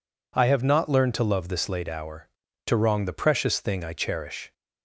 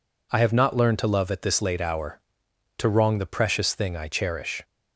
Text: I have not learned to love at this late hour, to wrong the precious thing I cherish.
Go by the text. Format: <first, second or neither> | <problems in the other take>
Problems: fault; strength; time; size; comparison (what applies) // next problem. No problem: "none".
second | skips "at"; at 1.4 s